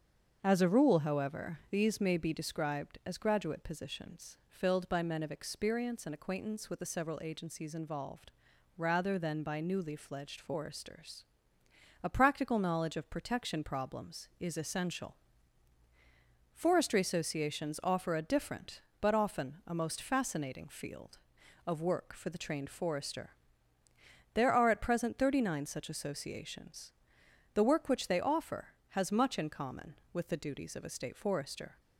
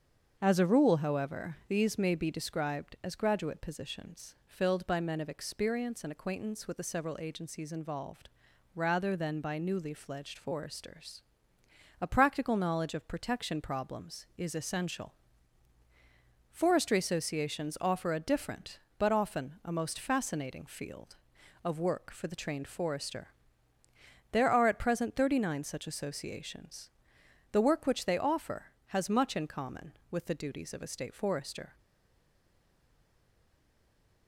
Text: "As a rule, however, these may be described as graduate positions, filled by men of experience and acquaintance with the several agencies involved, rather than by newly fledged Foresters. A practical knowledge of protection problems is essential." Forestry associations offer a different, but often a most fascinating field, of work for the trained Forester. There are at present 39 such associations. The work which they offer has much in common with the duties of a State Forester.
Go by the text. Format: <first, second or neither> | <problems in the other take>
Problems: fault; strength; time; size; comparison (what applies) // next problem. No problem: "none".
first | starts louder than the rest; until 1.4 s; 7 dB; also in the first // stays silent after the last word; strong; from 31.7 s on; 2.5 s long